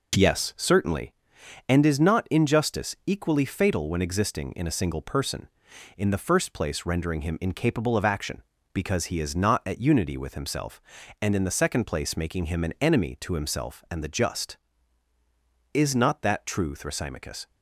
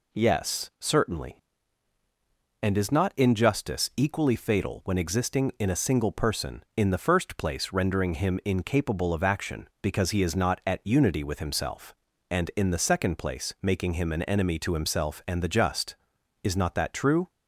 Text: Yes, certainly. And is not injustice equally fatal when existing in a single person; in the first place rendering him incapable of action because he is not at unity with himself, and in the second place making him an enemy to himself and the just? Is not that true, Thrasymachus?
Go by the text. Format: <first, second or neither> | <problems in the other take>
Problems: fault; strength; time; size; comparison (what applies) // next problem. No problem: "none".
first | stops before "Thrasymachus"; at 17.2 s